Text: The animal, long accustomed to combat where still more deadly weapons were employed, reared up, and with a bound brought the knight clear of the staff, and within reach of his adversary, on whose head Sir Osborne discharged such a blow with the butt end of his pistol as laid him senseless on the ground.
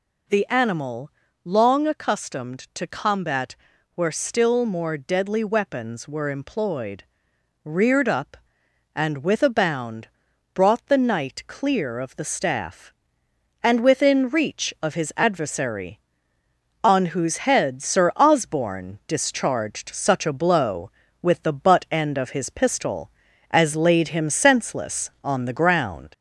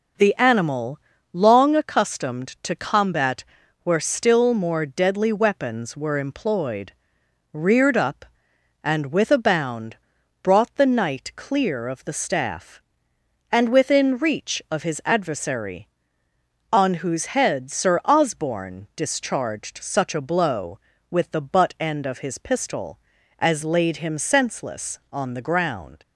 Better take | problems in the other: second | gets louder; slight; throughout; 2.5 dB // pauses between "combat" and "where"; at 3.5 s; 0.40 s long; also in the second // pauses between "bound" and "brought"; noticeable; at 10.0 s; 0.46 s long; noticeable in the second

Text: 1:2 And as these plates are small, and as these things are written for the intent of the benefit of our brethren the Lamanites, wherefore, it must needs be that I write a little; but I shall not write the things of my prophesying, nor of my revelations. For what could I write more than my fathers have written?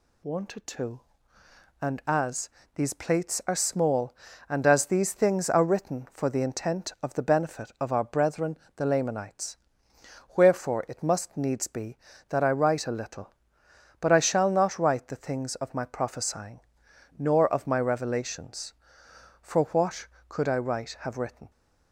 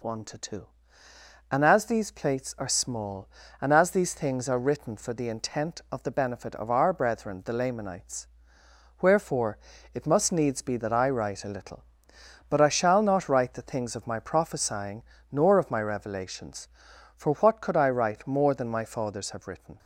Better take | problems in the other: second | pauses between "as" and "these"; slight; at 2.4 s; 0.28 s long // pauses between "brethren" and "the"; slight; at 8.5 s; 0.20 s long // skips "more than my fathers"; at 20.9 s

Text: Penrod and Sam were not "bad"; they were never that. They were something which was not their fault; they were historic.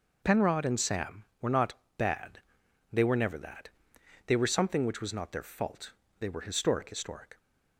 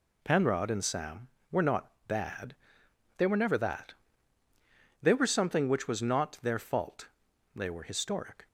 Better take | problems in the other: second | pauses between "not" and "bad"; slight; at 1.7 s; 0.24 s long; slight in the second // says "historic" twice; at 6.9 s

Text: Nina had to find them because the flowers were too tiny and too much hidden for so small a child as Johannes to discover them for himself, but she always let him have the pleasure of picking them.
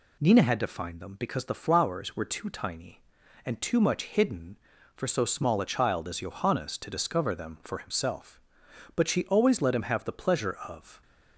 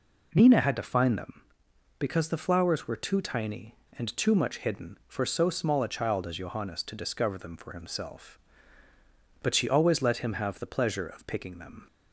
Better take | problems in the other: second | stops before "picking them"; at 11.0 s

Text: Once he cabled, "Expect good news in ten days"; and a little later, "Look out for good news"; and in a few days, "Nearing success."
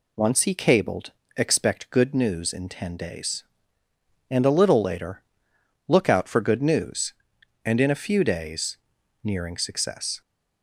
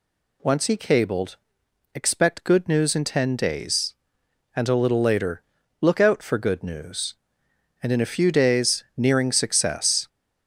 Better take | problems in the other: neither | none

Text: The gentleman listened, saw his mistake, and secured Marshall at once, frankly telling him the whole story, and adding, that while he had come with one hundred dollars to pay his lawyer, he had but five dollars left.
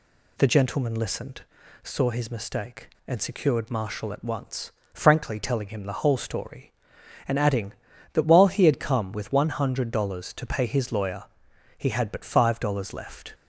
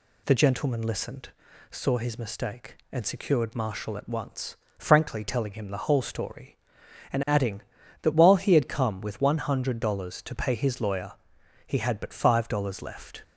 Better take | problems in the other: neither | none

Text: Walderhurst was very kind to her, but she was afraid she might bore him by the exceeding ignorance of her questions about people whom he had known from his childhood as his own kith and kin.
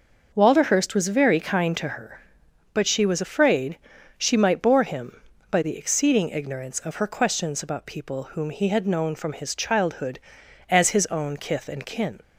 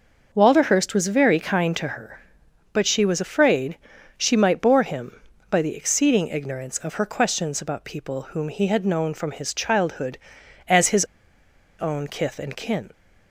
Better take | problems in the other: first | starts louder than the rest; until 1.3 s; 6.5 dB; also in the first // pauses between "afraid" and "she"; at 3.7 s; 0.40 s long; also in the first // pauses between "his" and "own"; noticeable; at 11.0 s; 0.75 s long

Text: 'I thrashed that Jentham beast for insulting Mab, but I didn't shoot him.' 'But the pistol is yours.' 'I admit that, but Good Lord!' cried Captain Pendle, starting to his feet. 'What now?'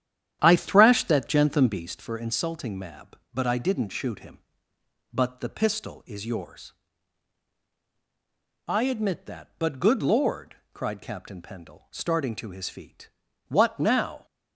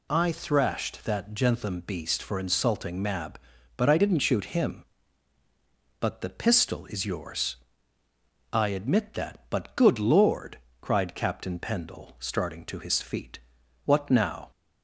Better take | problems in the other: second | starts louder than the rest; strong; until 1.9 s; 10.5 dB

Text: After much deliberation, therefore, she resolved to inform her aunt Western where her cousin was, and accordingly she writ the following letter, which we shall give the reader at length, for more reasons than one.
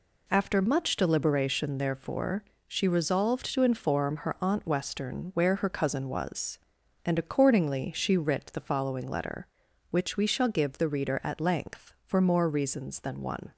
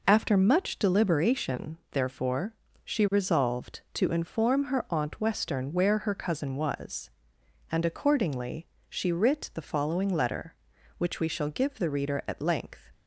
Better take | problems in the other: first | pauses between "accordingly" and "she"; slight; at 8.6 s; 0.22 s long // stops before "for more reasons than one"; at 12.9 s

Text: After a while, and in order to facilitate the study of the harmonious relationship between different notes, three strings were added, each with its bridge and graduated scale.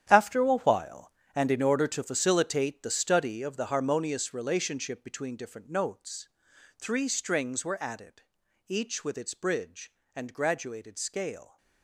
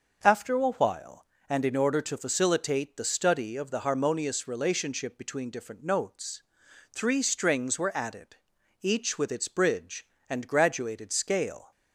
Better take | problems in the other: second | gets quieter; strong; throughout; 12.5 dB

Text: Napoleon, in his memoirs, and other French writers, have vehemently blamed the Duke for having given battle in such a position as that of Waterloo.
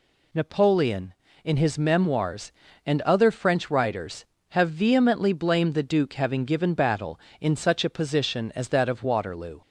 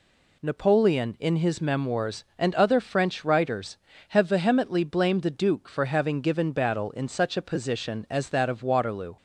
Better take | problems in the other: second | skips "for"; at 6.1 s

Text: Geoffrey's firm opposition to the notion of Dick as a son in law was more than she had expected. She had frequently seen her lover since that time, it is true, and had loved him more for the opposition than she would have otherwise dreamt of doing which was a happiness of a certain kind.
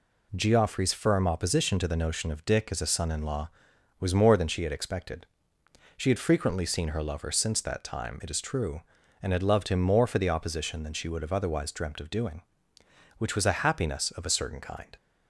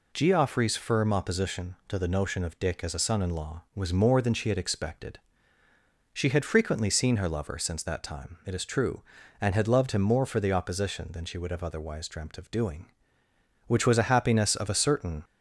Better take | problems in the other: first | stops before "kind"; at 15.2 s

